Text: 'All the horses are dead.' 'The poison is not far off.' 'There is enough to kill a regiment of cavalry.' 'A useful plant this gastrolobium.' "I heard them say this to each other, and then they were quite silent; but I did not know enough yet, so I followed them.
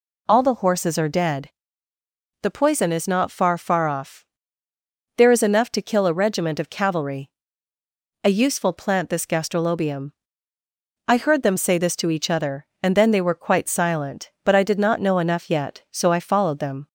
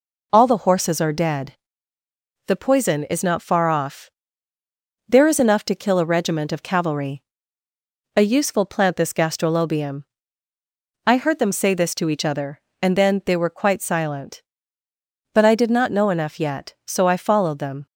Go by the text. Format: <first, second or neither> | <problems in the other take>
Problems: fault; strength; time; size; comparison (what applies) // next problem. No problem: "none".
second | says "far" twice; at 3.5 s